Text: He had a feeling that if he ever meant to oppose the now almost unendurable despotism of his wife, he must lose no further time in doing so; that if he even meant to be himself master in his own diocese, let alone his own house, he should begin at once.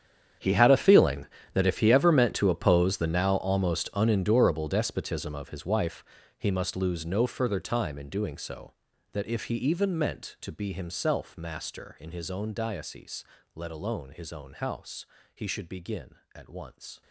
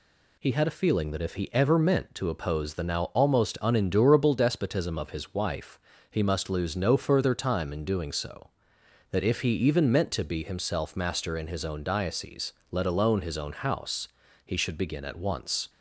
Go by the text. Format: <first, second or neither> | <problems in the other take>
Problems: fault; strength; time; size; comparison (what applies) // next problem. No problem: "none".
second | gets quieter; strong; throughout; 17.5 dB